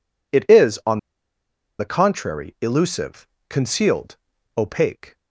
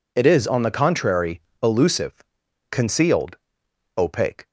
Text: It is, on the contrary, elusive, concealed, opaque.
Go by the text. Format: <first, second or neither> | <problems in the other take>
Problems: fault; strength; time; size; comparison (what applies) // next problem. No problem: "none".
second | pauses between "on" and "the"; noticeable; at 0.9 s; 0.81 s long